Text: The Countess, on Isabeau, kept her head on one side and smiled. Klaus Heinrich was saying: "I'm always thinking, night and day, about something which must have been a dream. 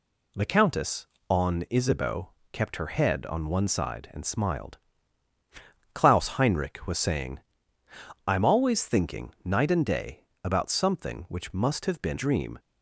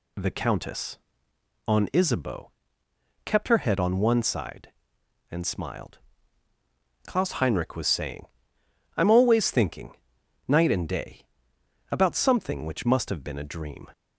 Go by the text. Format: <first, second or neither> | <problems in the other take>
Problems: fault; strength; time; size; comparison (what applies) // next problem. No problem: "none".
second | skips "a"; at 12.1 s